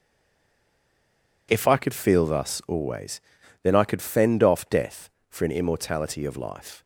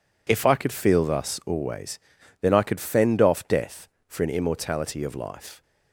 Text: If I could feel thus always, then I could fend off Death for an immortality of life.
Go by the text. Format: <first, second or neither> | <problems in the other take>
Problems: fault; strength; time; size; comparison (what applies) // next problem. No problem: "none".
second | stays silent before the first word; noticeable; until 1.4 s; 1.4 s long